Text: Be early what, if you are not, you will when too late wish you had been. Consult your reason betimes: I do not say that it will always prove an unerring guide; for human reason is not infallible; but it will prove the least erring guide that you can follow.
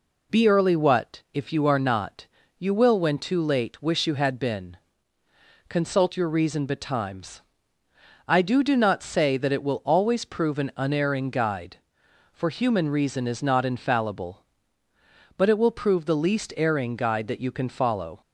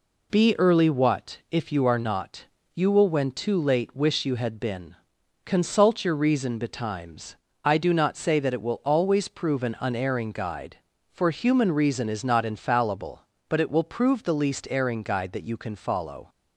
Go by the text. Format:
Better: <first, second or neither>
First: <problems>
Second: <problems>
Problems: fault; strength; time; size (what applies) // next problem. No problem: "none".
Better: second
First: says "do" twice; at 8.6 s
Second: none